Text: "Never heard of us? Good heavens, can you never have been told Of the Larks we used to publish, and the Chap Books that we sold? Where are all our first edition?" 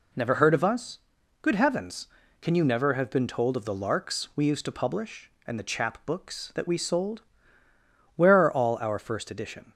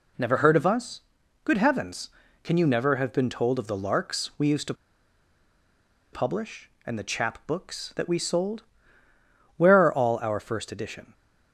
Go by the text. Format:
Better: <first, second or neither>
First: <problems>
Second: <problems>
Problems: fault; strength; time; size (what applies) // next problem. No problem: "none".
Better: first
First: none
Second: pauses between "to" and "publish"; strong; at 4.7 s; 1.3 s long